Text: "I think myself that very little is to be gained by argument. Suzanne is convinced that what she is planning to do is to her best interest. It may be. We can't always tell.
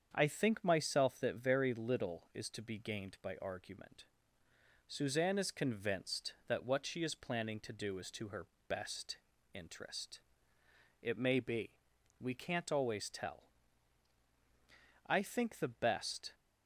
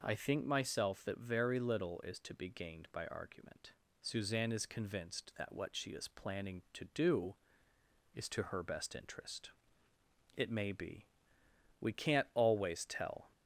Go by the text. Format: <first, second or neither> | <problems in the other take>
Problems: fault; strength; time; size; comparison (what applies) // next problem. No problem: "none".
second | starts louder than the rest; strong; until 1.1 s; 7.5 dB // pauses between "her" and "best"; slight; at 8.4 s; 0.22 s long // pauses between "best" and "interest"; slight; at 9.1 s; 0.36 s long // goes on to say "I think the best"; noticeable; from 15.0 s on; 1.2 s long